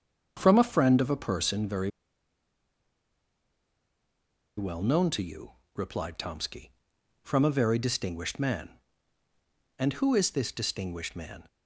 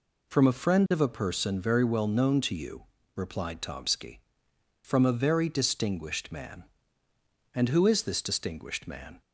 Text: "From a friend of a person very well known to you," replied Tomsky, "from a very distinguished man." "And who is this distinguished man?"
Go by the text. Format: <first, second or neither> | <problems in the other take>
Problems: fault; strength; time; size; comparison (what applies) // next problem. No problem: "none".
second | starts louder than the rest; until 1.3 s; 7 dB // pauses between "very" and "well"; strong; at 1.8 s; 2.6 s long